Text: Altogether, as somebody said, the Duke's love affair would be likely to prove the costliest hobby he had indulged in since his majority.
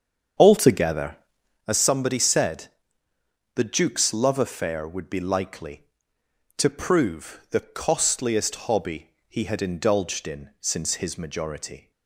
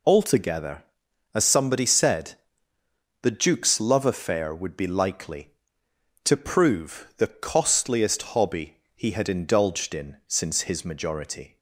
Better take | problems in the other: second | starts louder than the rest; strong; until 1.7 s; 7.5 dB // pauses between "hobby" and "he"; slight; at 9.1 s; 0.18 s long; slight in the second

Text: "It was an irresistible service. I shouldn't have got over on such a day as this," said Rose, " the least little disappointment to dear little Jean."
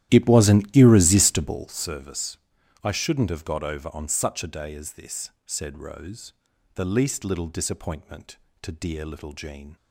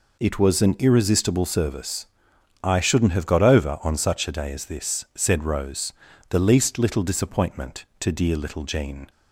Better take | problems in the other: second | starts louder than the rest; strong; until 1.8 s; 13 dB

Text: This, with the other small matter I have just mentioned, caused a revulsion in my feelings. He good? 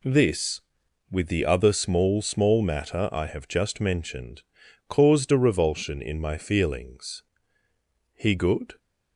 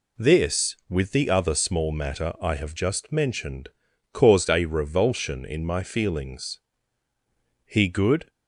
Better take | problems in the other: second | says "small" twice; at 2.2 s

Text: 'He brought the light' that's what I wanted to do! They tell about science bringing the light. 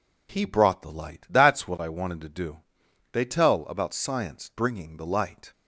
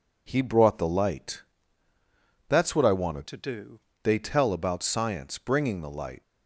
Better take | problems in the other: first | pauses between "light" and "that's"; at 1.4 s; 1.0 s long // changes voice from "to" to "do"; from 3.2 to 3.7 s; 0.5 s long

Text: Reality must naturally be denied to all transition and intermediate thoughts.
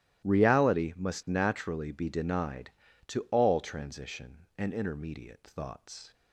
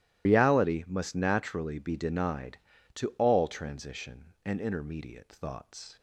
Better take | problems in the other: first | loses the start of "Reality"; at 0.2 s; 95 ms // starts louder than the rest; strong; until 1.3 s; 15 dB; strong in the first

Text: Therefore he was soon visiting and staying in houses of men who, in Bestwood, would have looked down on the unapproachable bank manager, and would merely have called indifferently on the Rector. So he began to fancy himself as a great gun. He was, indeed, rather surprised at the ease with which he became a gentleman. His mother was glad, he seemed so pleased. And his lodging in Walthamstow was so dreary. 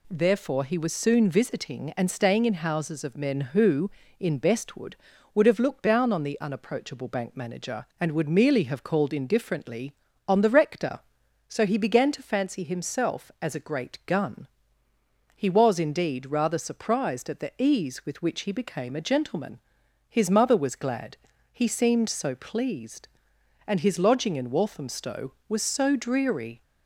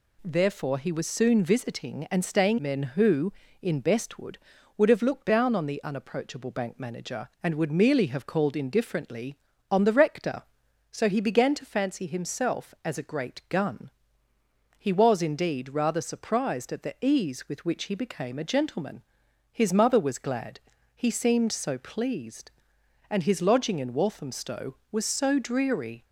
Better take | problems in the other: first | skips "in houses of"; at 2.5 s

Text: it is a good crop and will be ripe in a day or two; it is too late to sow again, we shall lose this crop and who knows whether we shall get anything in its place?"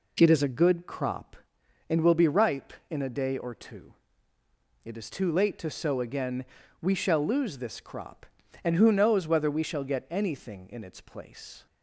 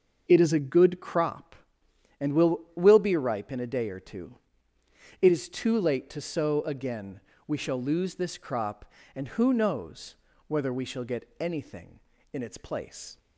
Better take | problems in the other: first | starts louder than the rest; until 1.2 s; 6 dB // says "will" twice; at 2.7 s // pauses between "knows" and "whether"; slight; at 10.1 s; 0.34 s long

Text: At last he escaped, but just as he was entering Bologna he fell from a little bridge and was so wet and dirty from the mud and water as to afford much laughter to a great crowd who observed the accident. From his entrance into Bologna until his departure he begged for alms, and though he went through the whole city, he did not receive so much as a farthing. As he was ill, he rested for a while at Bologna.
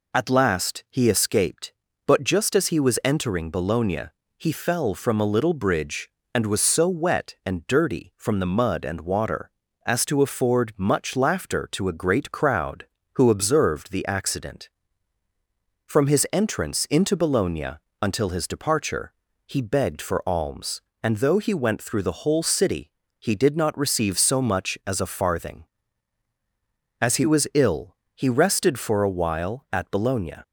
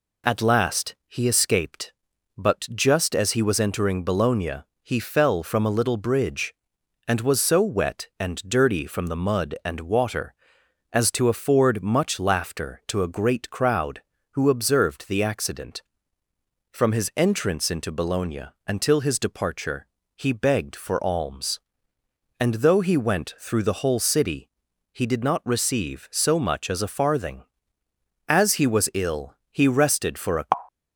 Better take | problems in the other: first | pauses between "Bologna" and "he"; slight; at 4.6 s; 0.18 s long; slight in the first // pauses between "Bologna" and "until"; slight; at 18.4 s; 0.22 s long; slight in the first // pauses between "departure" and "he"; slight; at 19.8 s; 0.32 s long; slight in the first // stops before "while at Bologna"; at 30.6 s

